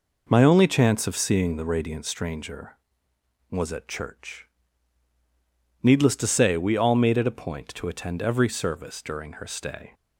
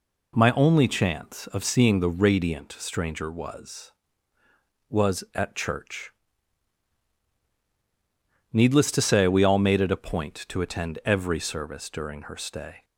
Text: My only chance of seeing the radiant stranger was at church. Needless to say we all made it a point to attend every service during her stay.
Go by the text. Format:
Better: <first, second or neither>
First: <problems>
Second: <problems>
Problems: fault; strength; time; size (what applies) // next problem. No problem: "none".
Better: first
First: none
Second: says "was" twice; at 4.9 s